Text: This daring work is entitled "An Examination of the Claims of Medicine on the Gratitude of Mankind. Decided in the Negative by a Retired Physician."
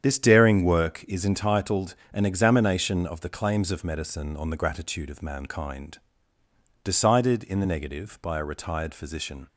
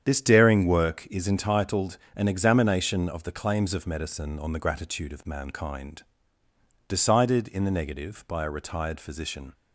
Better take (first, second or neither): neither